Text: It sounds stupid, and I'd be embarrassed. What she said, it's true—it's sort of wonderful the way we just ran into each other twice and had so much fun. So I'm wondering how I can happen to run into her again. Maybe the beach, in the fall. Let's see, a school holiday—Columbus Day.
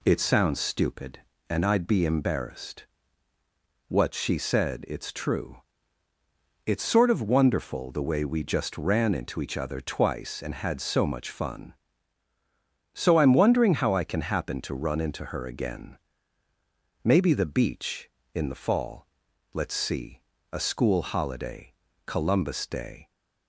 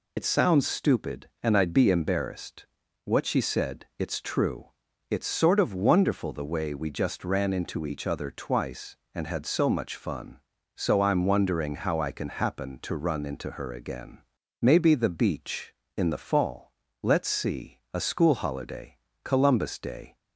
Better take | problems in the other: first | loses the start of "It"; at 0.1 s; 45 ms

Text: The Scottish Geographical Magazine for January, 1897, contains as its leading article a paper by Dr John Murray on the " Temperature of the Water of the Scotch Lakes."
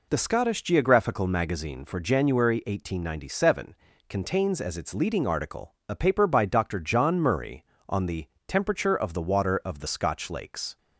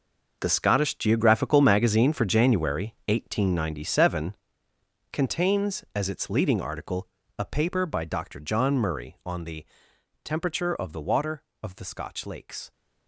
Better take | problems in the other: first | gets quieter; strong; throughout; 16 dB // pauses between "article" and "a"; slight; at 7.0 s; 0.30 s long

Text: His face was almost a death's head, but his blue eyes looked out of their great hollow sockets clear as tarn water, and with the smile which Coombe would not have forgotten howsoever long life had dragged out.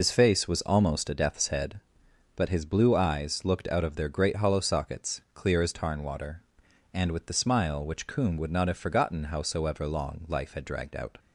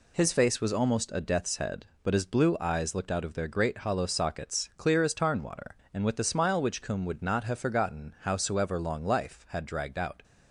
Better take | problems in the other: second | loses the start of "His"; at 0.0 s; 85 ms

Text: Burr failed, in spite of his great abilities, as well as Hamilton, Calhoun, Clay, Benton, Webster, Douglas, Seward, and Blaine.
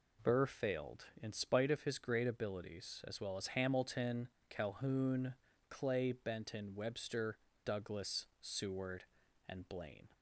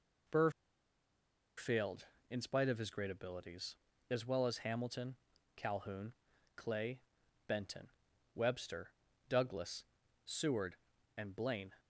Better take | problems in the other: first | pauses between "Burr" and "failed"; at 0.5 s; 1.0 s long

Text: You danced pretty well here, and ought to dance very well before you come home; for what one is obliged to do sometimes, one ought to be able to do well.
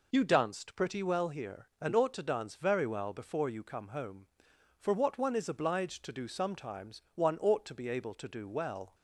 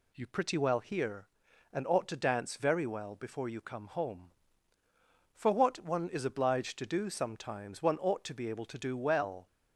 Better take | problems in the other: first | skips "danced"; at 0.2 s

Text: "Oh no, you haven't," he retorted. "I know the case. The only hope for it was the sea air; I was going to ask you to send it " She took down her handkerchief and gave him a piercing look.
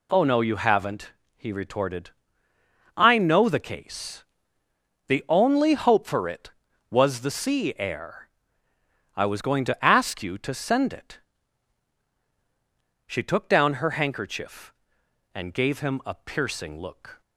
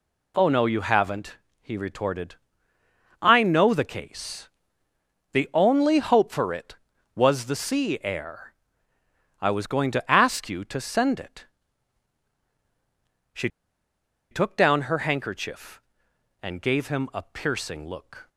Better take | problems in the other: first | pauses between "She" and "took"; noticeable; at 13.4 s; 0.83 s long

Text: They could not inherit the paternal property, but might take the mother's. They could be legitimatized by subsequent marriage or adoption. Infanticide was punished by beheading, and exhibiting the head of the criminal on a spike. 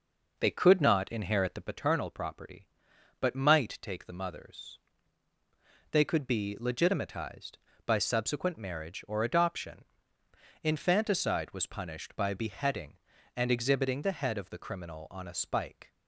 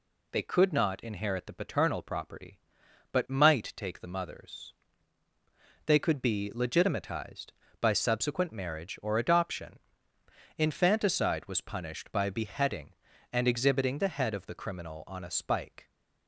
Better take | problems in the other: second | starts louder than the rest; noticeable; until 1.8 s; 5 dB

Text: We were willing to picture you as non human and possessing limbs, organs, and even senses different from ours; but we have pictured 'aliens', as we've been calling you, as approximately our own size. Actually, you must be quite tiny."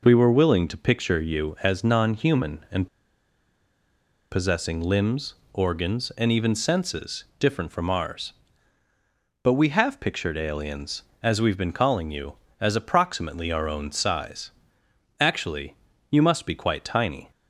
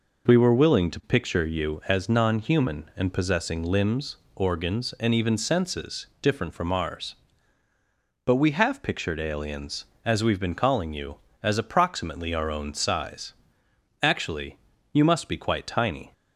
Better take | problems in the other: second | pauses between "and" and "possessing"; strong; at 2.8 s; 1.4 s long // pauses between "senses" and "different"; slight; at 7.2 s; 0.16 s long; slight in the second

